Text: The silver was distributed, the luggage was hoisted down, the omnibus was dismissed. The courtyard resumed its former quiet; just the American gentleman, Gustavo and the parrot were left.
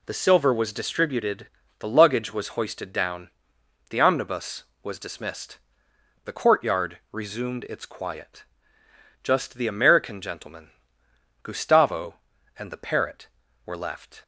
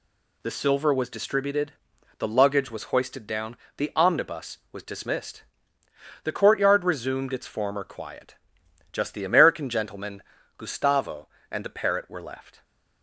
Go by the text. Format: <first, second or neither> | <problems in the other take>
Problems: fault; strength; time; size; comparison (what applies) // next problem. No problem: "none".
second | skips "former"; at 7.8 s